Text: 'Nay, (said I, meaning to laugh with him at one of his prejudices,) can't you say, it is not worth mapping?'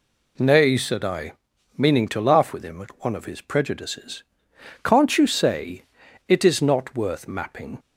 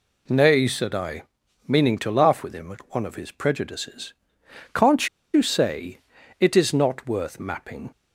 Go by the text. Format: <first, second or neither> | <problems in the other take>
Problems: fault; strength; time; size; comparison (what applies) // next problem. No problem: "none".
first | pauses between "can't" and "you"; slight; at 5.0 s; 0.26 s long